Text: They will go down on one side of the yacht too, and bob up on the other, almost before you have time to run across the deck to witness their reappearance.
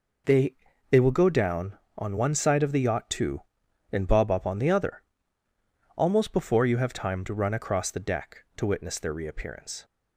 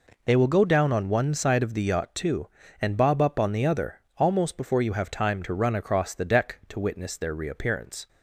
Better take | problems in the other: second | says "They" twice; at 0.8 s

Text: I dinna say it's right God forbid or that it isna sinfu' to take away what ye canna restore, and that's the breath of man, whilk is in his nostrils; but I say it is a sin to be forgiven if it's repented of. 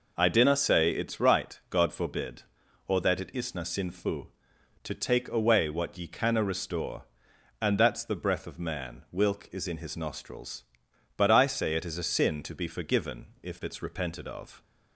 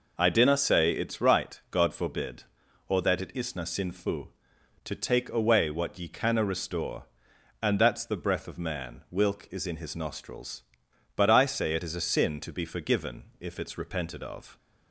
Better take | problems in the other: neither | none

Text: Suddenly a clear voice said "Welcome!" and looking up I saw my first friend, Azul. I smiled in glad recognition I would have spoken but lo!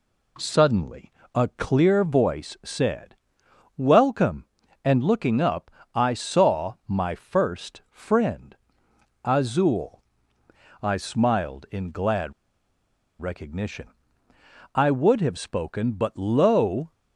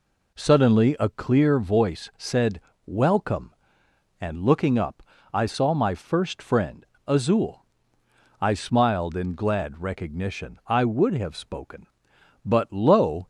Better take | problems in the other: second | pauses between "Suddenly" and "a"; slight; at 1.1 s; 0.22 s long // pauses between "said" and "Welcome"; noticeable; at 3.1 s; 0.60 s long; slight in the second // pauses between "up" and "I"; slight; at 5.7 s; 0.24 s long; slight in the second // pauses between "glad" and "recognition"; noticeable; at 12.3 s; 0.88 s long // pauses between "recognition" and "I"; noticeable; at 13.8 s; 0.88 s long

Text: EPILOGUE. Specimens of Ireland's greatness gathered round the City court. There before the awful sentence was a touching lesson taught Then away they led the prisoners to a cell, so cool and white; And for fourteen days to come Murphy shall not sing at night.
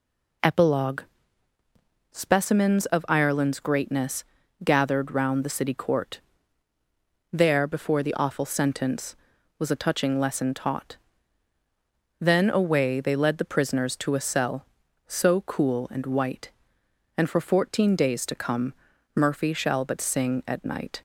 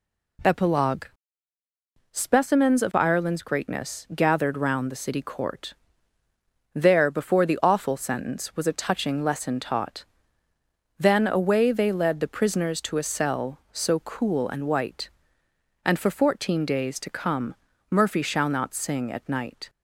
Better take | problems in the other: second | pauses between "greatness" and "gathered"; at 4.2 s; 0.40 s long // pauses between "taught" and "Then"; strong; at 10.9 s; 1.2 s long; noticeable in the second // pauses between "come" and "Murphy"; at 18.7 s; 0.42 s long; also in the second // says "but" for "not"; at 19.8 s

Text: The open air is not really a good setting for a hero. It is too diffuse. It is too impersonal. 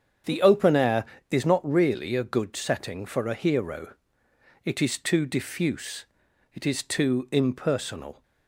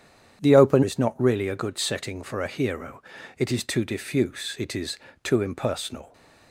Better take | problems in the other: first | starts louder than the rest; strong; until 1.4 s; 9 dB; strong in the first // skips "air"; at 0.8 s // pauses between "is" and "too"; slight; at 4.9 s; 0.28 s long

